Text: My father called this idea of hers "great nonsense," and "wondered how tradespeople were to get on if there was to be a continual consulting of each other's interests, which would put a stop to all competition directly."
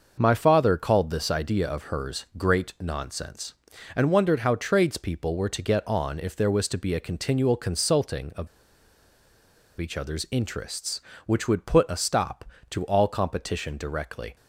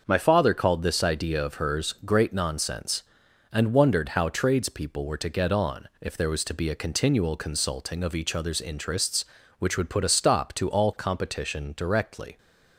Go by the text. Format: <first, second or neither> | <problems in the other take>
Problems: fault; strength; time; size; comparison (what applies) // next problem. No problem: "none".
second | starts louder than the rest; noticeable; until 1.2 s; 6 dB; also in the second // pauses between "of" and "each"; strong; at 8.4 s; 1.3 s long